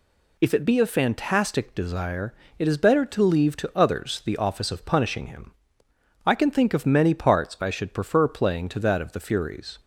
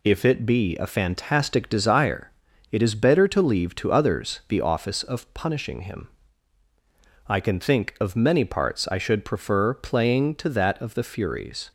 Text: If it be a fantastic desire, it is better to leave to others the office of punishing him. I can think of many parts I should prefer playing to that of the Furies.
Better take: neither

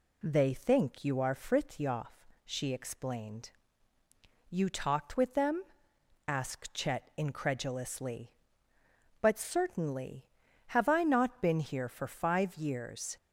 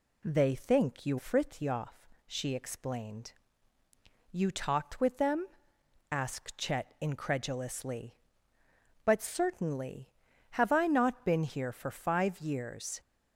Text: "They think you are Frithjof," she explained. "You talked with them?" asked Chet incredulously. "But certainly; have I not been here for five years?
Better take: first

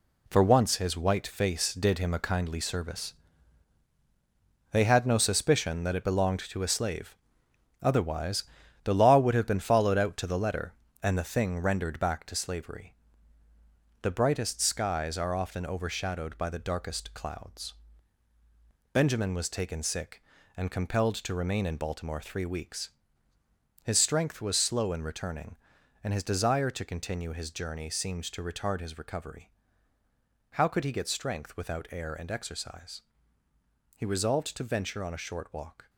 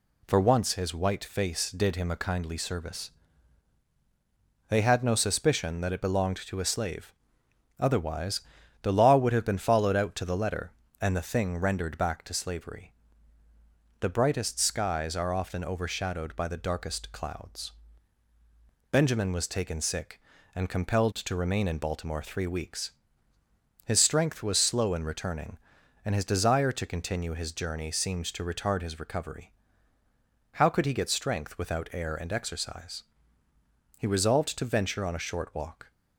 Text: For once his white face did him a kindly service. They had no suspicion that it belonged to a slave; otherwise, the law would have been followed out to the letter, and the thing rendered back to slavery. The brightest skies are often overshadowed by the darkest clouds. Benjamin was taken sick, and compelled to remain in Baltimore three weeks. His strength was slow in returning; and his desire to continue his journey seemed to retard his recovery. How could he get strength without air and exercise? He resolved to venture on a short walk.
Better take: second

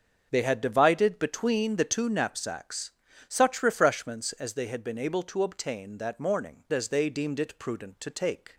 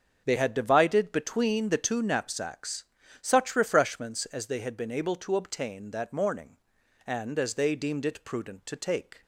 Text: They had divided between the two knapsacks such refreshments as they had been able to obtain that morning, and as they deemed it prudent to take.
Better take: second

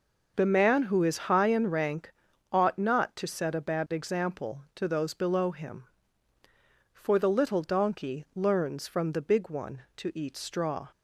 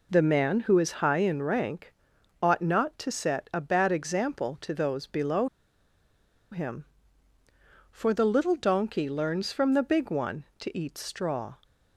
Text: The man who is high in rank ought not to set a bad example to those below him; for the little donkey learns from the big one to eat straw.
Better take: first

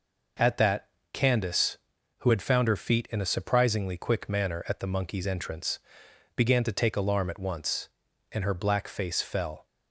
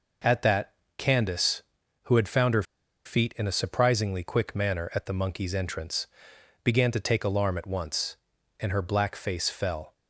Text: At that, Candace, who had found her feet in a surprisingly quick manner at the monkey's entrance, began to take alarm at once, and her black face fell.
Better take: first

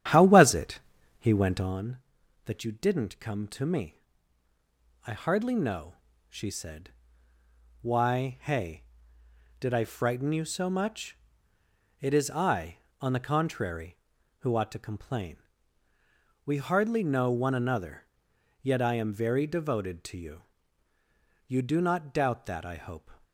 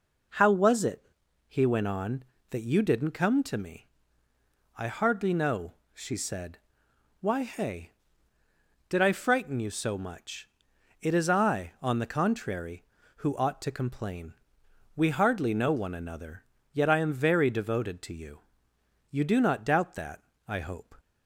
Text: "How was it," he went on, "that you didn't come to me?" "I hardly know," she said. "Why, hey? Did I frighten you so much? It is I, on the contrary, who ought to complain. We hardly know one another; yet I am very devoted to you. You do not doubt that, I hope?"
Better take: second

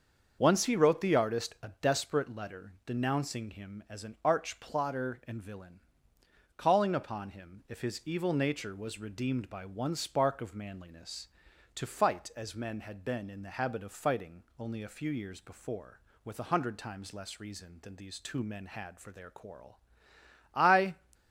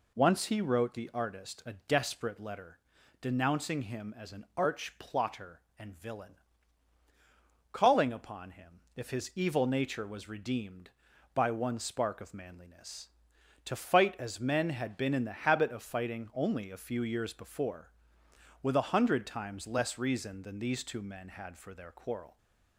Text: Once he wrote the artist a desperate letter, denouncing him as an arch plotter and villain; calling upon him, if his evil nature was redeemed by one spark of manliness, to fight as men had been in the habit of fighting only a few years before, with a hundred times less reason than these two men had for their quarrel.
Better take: second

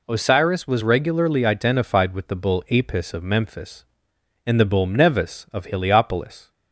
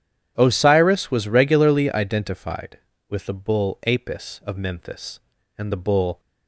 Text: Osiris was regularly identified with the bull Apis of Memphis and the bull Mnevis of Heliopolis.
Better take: first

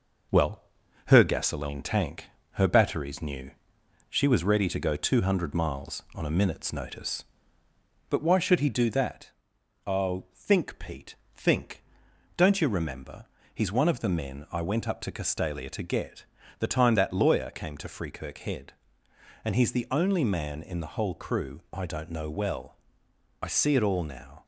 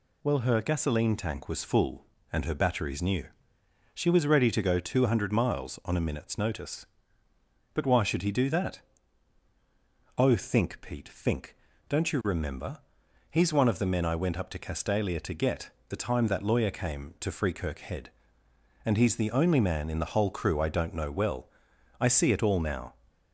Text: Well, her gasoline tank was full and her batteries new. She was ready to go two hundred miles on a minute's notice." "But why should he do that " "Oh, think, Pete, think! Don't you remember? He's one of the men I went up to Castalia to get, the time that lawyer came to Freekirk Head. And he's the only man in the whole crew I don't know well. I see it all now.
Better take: second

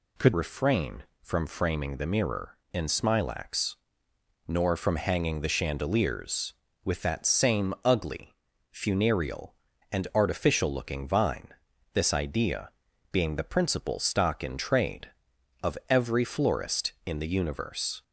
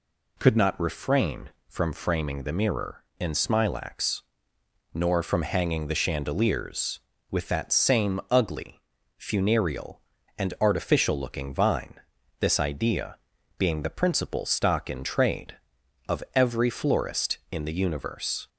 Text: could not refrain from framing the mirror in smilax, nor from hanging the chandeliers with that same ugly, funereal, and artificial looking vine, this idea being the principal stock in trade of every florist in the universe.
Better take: second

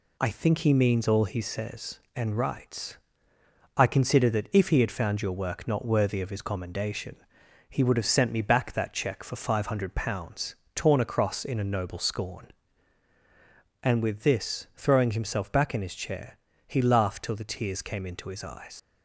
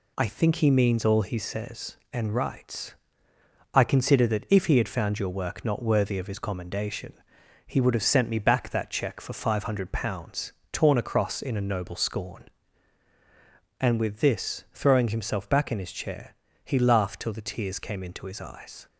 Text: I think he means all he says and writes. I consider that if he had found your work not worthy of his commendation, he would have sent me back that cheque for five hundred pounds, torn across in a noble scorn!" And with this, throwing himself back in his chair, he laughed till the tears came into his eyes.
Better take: second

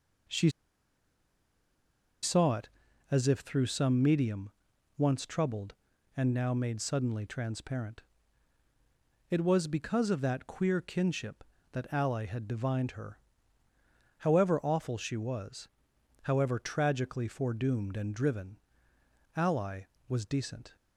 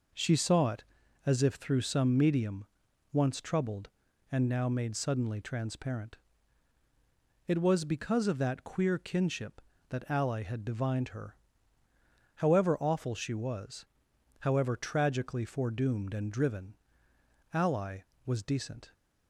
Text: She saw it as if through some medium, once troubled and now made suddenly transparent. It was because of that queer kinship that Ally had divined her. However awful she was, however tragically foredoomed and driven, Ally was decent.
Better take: second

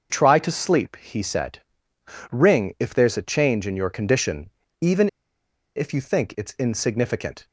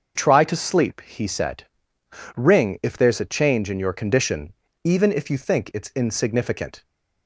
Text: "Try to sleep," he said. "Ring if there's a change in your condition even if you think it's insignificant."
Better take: second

